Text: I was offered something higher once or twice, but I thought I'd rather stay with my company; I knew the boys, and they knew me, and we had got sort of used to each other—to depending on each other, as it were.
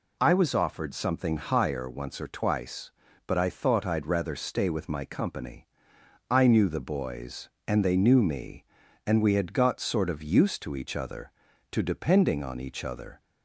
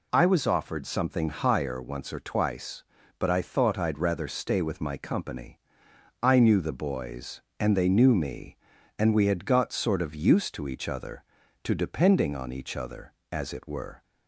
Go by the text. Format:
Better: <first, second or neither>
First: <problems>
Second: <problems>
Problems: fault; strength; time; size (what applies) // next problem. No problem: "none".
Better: second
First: stops before "as it were"; at 13.1 s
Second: none